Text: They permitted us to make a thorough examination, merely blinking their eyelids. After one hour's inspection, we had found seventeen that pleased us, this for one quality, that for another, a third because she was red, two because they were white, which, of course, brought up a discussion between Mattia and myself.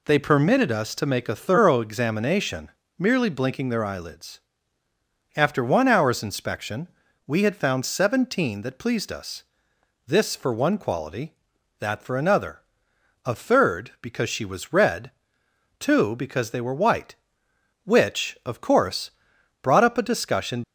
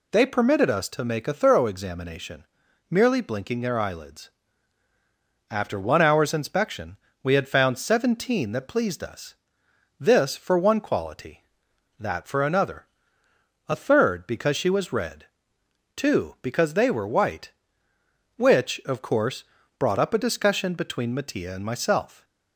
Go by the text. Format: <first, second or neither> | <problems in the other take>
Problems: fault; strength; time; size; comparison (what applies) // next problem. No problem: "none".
second | stops before "between Mattia and myself"; at 20.6 s